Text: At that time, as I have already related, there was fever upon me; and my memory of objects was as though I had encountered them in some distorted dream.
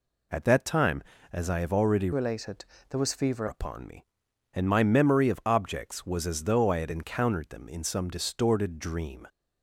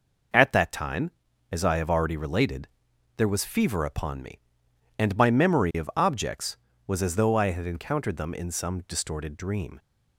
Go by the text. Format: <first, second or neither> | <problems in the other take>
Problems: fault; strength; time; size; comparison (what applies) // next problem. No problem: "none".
second | changes voice from "related" to "fever"; from 2.1 to 3.4 s; 1.3 s long